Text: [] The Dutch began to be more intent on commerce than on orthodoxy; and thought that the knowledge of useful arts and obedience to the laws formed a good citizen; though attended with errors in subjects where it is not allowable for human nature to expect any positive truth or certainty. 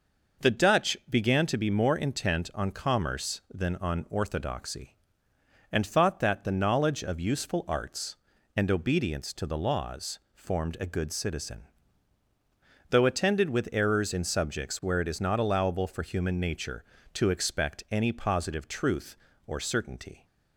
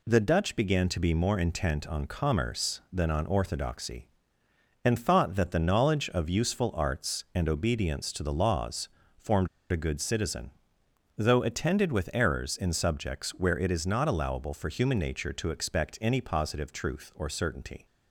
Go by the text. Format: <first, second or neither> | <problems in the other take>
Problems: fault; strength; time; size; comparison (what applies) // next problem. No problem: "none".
first | pauses between "laws" and "formed"; slight; at 8.8 s; 0.28 s long // pauses between "formed" and "a"; slight; at 9.4 s; 0.22 s long